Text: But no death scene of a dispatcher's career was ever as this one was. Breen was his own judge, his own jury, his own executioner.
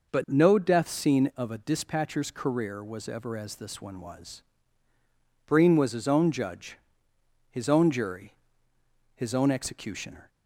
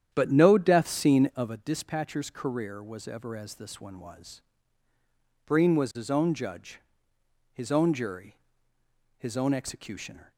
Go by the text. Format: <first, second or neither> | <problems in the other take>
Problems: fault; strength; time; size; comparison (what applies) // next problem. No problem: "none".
first | starts louder than the rest; strong; until 1.6 s; 9.5 dB